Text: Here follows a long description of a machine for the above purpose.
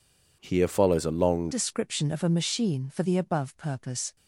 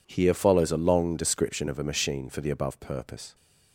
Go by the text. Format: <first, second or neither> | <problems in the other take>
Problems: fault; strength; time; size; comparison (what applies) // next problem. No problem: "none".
second | changes voice at "description"; from 1.5 s on; 2.6 s long